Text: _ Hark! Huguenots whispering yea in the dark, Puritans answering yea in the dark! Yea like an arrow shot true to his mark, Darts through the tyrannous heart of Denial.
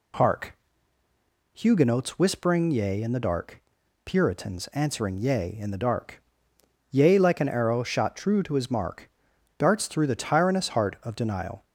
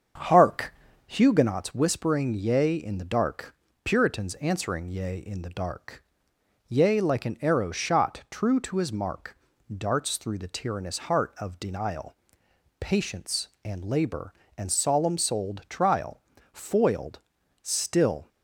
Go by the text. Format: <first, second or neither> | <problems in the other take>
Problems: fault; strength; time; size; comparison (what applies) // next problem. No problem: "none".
first | starts louder than the rest; until 1.5 s; 7 dB // goes on to say "Patience and Labor and solemn souled Trial Foiled still"; strong; from 12.8 s on; 5.4 s long